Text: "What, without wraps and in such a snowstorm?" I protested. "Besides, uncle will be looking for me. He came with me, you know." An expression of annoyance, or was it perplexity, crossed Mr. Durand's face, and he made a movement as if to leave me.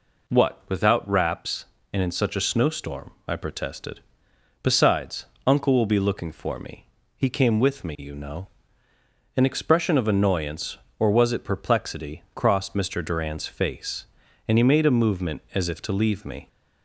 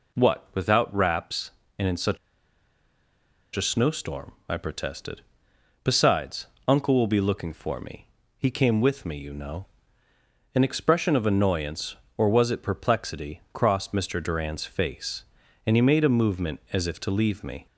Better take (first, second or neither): first